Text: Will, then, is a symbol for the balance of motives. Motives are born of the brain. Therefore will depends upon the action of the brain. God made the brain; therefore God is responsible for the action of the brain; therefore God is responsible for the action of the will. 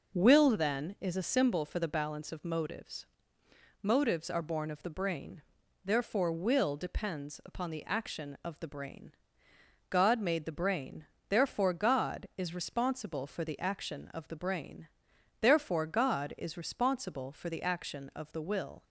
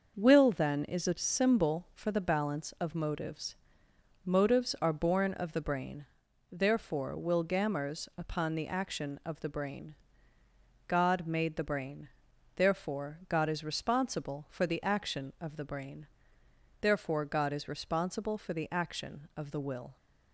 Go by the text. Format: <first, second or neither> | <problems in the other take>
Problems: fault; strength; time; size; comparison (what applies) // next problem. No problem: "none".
first | starts louder than the rest; noticeable; until 1.1 s; 6 dB // says "gammers" for "depends"; at 7.4 s